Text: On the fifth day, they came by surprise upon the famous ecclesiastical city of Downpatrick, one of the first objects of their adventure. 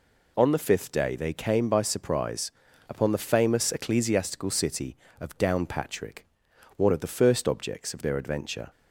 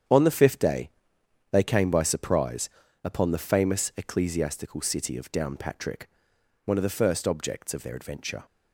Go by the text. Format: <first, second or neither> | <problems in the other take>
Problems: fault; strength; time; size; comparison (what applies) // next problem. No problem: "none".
first | gets quieter; strong; throughout; 9 dB // pauses between "surprise" and "upon"; slight; at 2.6 s; 0.34 s long; slight in the first